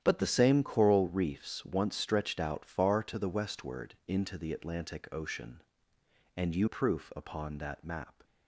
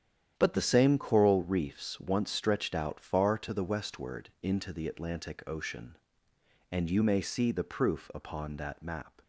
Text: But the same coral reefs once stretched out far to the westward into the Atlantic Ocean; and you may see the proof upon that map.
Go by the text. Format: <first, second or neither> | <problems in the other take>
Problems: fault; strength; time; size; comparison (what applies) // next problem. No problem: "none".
second | starts louder than the rest; strong; until 1.0 s; 10.5 dB; strong in the second // skips "may see the"; at 6.6 s